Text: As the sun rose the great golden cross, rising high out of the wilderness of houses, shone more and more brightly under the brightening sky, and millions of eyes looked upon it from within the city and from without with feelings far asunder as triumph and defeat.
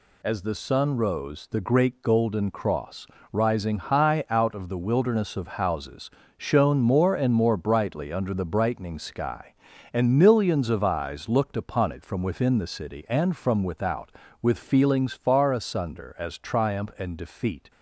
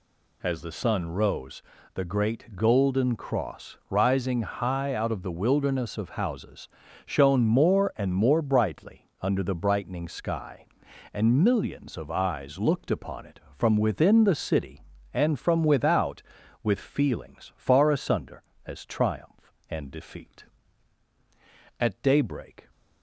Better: first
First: none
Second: pauses between "rose" and "the"; slight; at 1.6 s; 0.34 s long // goes on to say "At daybreak"; noticeable; from 21.8 s on; 0.88 s long

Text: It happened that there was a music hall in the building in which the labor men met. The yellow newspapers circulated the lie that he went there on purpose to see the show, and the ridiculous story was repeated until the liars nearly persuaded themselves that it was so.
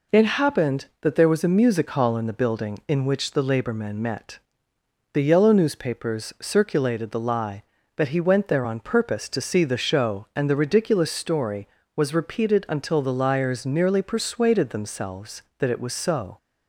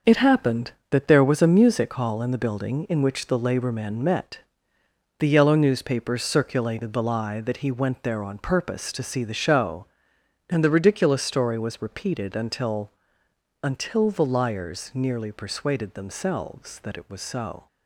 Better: first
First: none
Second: starts louder than the rest; noticeable; until 1.2 s; 6 dB // says "until" twice; at 13.6 s

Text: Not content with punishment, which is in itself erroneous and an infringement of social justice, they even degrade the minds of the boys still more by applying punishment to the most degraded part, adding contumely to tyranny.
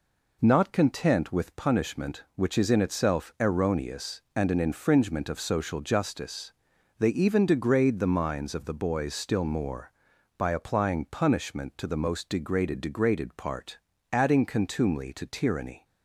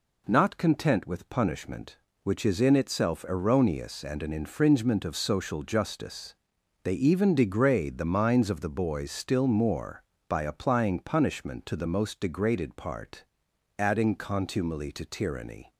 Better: second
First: says "degraded" twice; at 12.7 s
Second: none

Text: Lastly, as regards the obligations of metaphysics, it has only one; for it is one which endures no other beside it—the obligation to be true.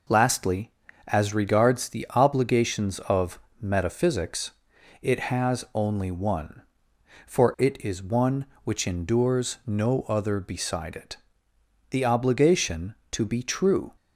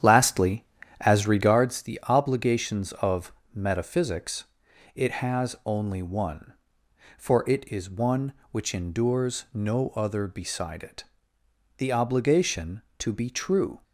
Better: first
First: pauses between "of" and "metaphysics"; slight; at 3.3 s; 0.20 s long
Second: starts louder than the rest; strong; until 1.6 s; 9.5 dB // pauses between "of" and "metaphysics"; slight; at 3.3 s; 0.20 s long

